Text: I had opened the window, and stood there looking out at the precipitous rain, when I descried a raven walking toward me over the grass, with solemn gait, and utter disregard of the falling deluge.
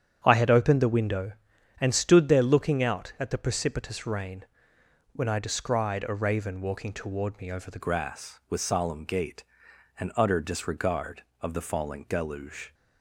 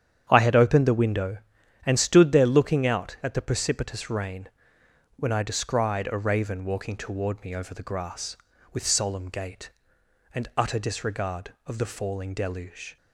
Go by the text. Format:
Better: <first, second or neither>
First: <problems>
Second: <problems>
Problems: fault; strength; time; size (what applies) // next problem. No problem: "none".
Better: second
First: starts louder than the rest; strong; until 1.2 s; 8 dB // changes voice at "grass"; from 7.8 s on; 4.9 s long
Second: starts louder than the rest; strong; until 1.3 s; 8.5 dB